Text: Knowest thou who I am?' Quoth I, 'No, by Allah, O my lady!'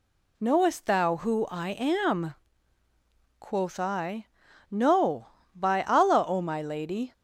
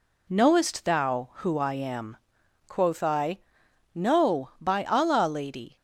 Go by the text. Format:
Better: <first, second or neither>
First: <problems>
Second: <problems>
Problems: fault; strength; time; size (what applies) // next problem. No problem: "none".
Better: first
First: none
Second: skips "O my"; at 5.2 s